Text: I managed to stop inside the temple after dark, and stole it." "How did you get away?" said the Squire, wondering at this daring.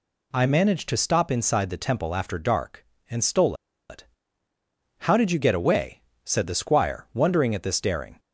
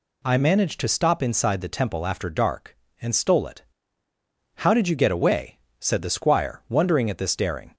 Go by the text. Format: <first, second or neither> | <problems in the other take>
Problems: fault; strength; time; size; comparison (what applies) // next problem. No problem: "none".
second | pauses between "stole" and "it"; slight; at 3.5 s; 0.36 s long